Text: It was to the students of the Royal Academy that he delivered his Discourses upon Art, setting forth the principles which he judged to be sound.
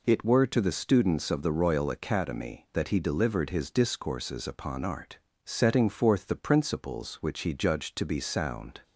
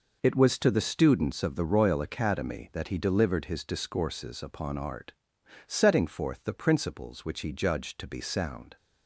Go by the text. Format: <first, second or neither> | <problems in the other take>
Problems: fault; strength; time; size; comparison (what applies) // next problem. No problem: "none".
second | says "were" for "was"; at 0.2 s